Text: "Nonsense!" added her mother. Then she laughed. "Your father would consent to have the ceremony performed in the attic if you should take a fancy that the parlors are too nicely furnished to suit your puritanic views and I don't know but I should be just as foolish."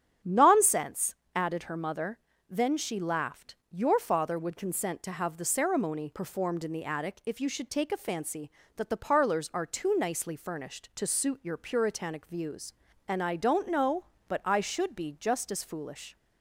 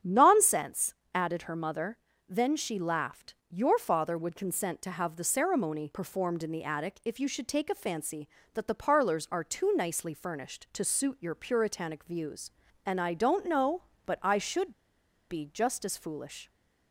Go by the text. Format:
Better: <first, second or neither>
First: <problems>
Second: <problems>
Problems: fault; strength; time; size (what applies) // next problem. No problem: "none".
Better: first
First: starts louder than the rest; strong; until 1.4 s; 8.5 dB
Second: starts louder than the rest; strong; until 1.2 s; 8.5 dB // pauses between "should" and "be"; noticeable; at 14.7 s; 0.56 s long